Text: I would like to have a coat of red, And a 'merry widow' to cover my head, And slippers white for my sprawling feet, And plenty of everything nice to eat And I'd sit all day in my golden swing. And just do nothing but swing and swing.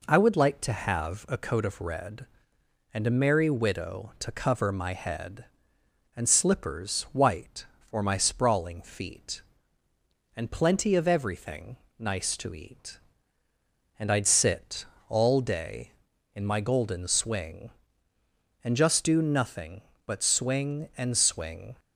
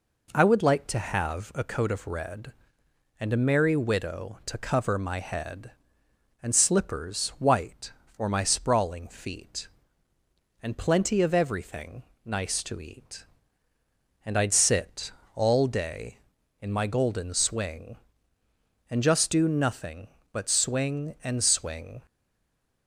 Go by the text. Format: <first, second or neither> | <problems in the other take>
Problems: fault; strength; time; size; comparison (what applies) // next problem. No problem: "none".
first | pauses between "everything" and "nice"; slight; at 12.0 s; 0.22 s long; slight in the first // pauses between "sit" and "all"; slight; at 15.1 s; 0.22 s long; slight in the first // stays silent after the last word; slight; from 22.0 s on; 0.8 s long